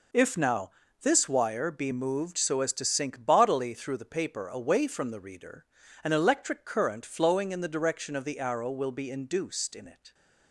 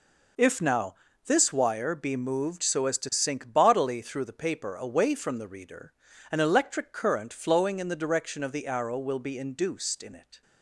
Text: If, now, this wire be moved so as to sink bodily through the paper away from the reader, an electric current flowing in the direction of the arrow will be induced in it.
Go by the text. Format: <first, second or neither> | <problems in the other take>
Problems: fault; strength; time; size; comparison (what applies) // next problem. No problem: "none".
neither | none